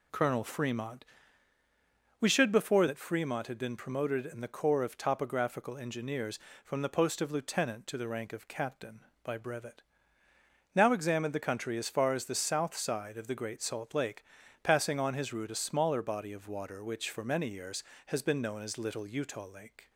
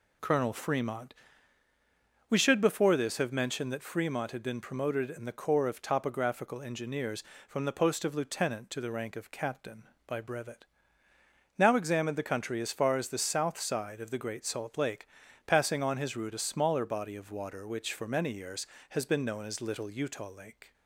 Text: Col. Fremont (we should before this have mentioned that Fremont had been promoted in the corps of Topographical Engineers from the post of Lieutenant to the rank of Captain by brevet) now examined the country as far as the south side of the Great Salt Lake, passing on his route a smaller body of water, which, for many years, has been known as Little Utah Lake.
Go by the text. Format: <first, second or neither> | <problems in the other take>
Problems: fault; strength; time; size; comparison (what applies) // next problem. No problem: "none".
second | skips "this have mentioned"; at 2.8 s